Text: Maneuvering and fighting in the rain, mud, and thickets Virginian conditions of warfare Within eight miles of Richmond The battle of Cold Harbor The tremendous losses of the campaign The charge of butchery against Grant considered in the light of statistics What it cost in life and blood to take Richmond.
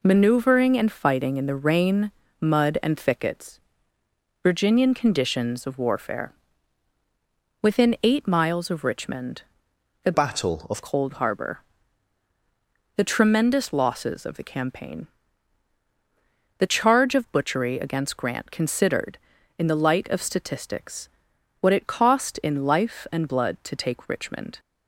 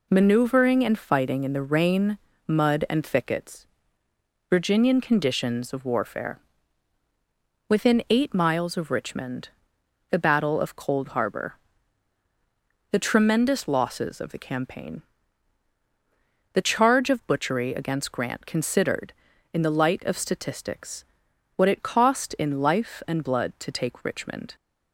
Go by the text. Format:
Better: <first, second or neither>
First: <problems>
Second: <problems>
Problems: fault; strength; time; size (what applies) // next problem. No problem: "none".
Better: second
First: pauses between "thickets" and "Virginian"; noticeable; at 3.5 s; 0.82 s long // pauses between "warfare" and "Within"; strong; at 6.3 s; 1.3 s long // pauses between "Richmond" and "The"; noticeable; at 9.4 s; 0.58 s long // changes voice from "battle" to "of"; from 10.1 to 10.8 s; 0.7 s long // pauses between "Harbor" and "The"; strong; at 11.6 s; 1.3 s long // pauses between "campaign" and "The"; strong; at 15.0 s; 1.5 s long // pauses between "statistics" and "What"; noticeable; at 21.0 s; 0.50 s long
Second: pauses between "thickets" and "Virginian"; noticeable; at 3.6 s; 0.82 s long // pauses between "warfare" and "Within"; strong; at 6.3 s; 1.3 s long // pauses between "Richmond" and "The"; noticeable; at 9.5 s; 0.58 s long // pauses between "Harbor" and "The"; strong; at 11.5 s; 1.3 s long // pauses between "campaign" and "The"; strong; at 15.0 s; 1.5 s long // pauses between "statistics" and "What"; noticeable; at 21.0 s; 0.50 s long